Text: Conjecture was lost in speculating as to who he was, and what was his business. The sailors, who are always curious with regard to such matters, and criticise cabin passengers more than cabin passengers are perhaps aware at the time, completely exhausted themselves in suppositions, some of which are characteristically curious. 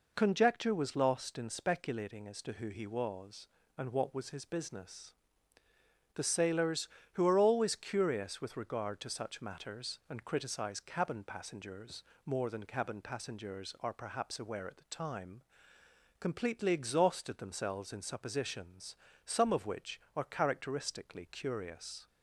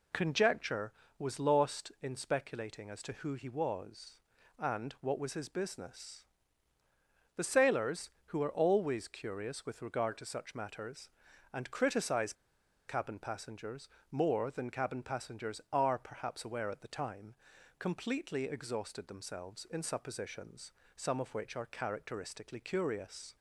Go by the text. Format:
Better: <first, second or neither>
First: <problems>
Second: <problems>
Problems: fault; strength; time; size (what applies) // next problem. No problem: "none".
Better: first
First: pauses between "passengers" and "more"; slight; at 12.0 s; 0.22 s long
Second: pauses between "criticise" and "cabin"; noticeable; at 12.3 s; 0.55 s long // pauses between "passengers" and "more"; slight; at 13.8 s; 0.24 s long